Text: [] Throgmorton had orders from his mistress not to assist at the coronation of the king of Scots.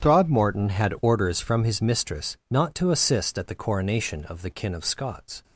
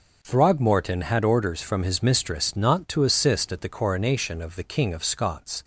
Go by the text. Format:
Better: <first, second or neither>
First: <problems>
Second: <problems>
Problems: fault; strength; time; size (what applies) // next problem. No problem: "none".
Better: second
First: starts louder than the rest; strong; until 1.0 s; 9.5 dB // says "kin" for "king"; at 4.4 s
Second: none